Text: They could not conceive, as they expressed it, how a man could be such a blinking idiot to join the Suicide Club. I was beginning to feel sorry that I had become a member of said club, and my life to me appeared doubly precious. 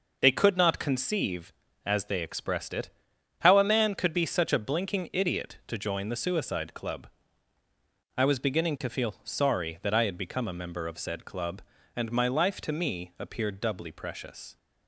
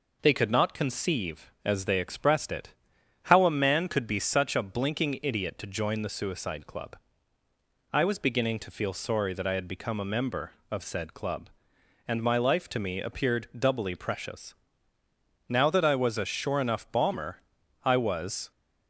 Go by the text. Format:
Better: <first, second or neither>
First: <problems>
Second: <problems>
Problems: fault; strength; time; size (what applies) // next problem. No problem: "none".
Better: first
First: none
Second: goes on to say "Now that I was a sure enough bomber I was"; strong; from 15.4 s on; 3.0 s long